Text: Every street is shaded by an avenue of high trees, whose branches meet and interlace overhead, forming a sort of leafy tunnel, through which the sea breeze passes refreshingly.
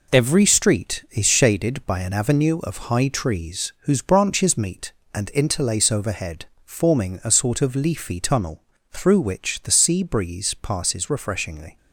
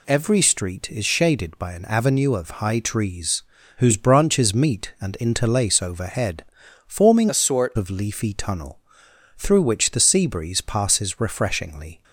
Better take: first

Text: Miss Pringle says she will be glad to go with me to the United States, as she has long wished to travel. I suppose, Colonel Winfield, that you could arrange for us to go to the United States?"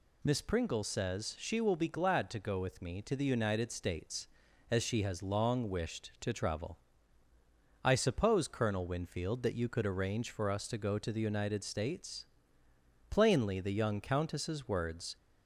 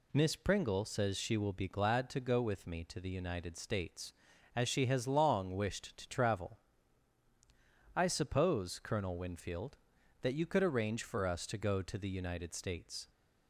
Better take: second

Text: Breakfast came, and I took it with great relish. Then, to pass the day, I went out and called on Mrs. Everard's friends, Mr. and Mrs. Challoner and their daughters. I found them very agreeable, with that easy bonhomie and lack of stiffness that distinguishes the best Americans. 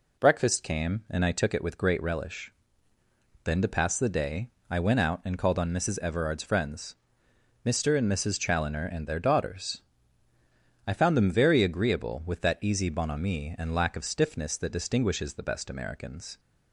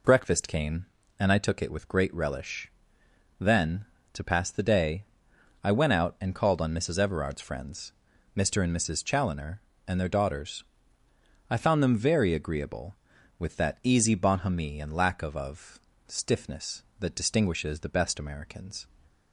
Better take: first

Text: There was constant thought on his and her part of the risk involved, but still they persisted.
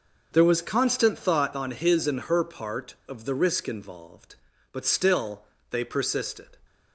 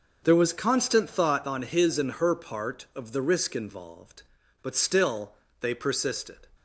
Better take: neither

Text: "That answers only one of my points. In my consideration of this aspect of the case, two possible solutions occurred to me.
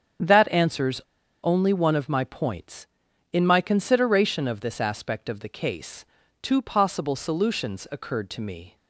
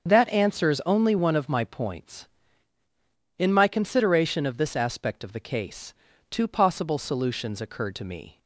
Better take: second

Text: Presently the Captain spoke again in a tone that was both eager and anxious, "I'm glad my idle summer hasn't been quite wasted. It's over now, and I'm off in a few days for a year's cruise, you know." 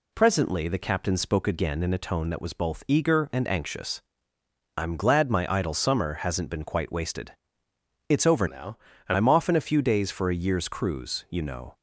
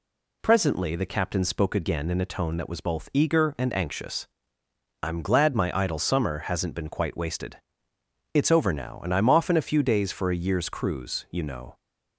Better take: second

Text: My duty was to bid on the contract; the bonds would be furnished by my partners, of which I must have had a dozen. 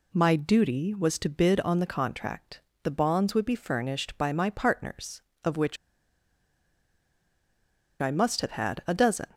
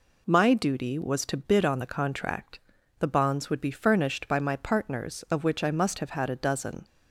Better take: second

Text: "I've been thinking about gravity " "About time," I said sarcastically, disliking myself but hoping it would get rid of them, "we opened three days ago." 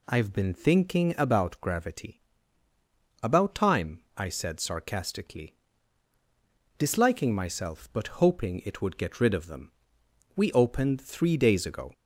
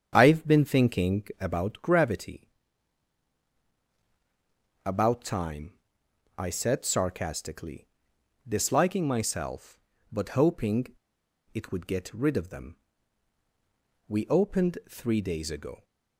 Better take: first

